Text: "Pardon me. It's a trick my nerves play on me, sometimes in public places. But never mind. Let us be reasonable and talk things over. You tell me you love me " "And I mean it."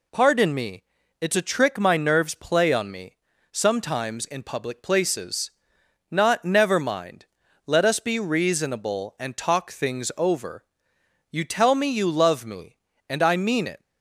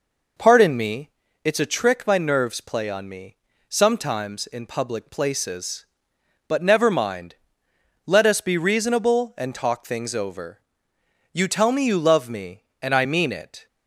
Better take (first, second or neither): second